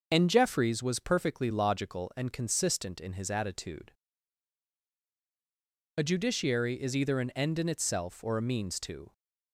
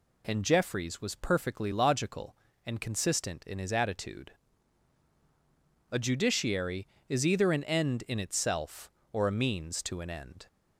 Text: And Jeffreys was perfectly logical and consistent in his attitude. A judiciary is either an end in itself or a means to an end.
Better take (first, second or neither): second